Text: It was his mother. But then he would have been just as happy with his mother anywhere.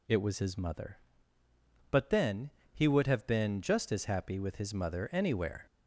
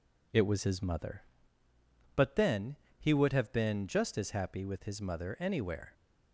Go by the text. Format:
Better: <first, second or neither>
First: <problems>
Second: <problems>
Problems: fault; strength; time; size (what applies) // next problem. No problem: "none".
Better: second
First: gets louder; slight; throughout; 2.5 dB // pauses between "then" and "he"; slight; at 2.4 s; 0.24 s long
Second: pauses between "then" and "he"; slight; at 2.7 s; 0.24 s long